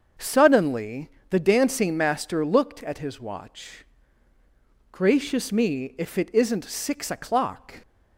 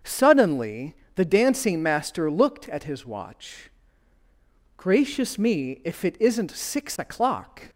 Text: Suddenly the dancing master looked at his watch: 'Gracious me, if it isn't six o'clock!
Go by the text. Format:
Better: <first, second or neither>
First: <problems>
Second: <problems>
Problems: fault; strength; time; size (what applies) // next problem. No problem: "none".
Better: neither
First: starts louder than the rest; until 1.3 s; 6.5 dB // pauses between "Suddenly" and "the"; slight; at 1.0 s; 0.20 s long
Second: starts louder than the rest; until 1.2 s; 7 dB // pauses between "Suddenly" and "the"; slight; at 0.9 s; 0.20 s long